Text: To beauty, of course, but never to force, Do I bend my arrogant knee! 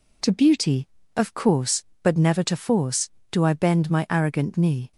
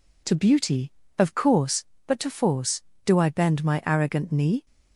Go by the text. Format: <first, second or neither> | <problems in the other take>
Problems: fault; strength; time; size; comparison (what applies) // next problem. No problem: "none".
first | skips "never"; at 2.1 s